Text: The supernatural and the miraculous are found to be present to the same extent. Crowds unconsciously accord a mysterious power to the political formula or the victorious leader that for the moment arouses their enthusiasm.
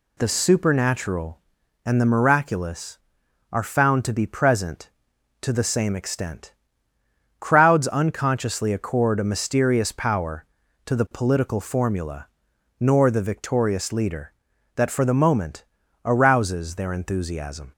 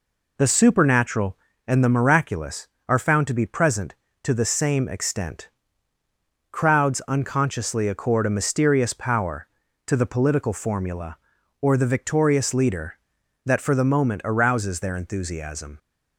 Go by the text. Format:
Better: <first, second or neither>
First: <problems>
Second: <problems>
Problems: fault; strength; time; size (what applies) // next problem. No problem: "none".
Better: second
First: says "nor" for "or"; at 12.7 s // pauses between "moment" and "arouses"; at 15.6 s; 0.40 s long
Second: none